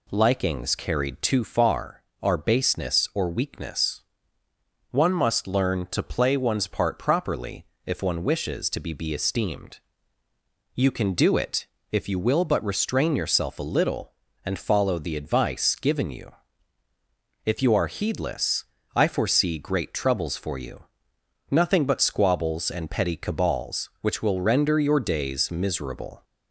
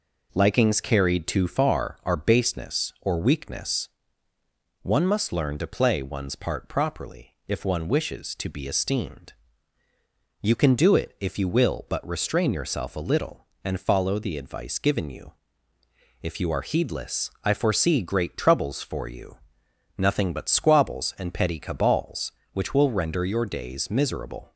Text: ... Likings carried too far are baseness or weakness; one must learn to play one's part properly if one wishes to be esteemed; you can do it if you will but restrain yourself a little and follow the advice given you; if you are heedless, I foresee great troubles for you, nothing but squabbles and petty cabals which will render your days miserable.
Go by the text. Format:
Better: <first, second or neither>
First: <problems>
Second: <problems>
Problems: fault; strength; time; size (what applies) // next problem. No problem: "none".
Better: second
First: pauses between "properly" and "if"; slight; at 7.6 s; 0.18 s long // says "be" twice; at 8.9 s // pauses between "it" and "if"; slight; at 11.6 s; 0.26 s long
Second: none